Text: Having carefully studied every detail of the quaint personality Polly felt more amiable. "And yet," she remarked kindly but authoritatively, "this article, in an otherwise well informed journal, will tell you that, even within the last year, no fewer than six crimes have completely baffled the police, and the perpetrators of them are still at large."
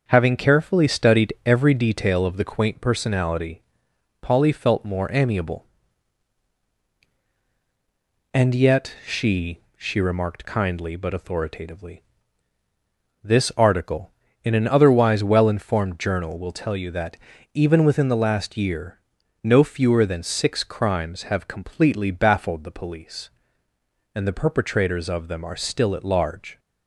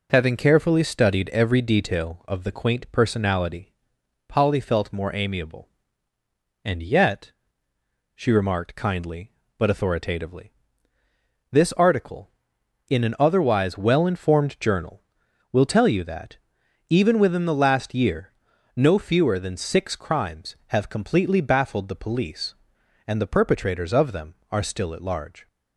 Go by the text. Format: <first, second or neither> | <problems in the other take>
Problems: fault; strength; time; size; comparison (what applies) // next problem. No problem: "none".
second | starts louder than the rest; noticeable; until 1.0 s; 6 dB // pauses between "personality" and "Polly"; noticeable; at 3.6 s; 0.60 s long; noticeable in the second // says "she" twice; at 9.7 s